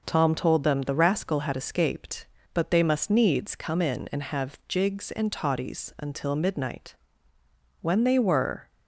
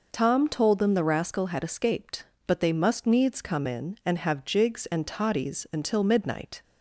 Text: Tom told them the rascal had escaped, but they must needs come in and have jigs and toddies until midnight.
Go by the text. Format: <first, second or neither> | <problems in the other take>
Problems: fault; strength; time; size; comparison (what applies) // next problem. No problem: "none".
second | goes on to say "When they were"; noticeable; from 7.7 s on; 0.88 s long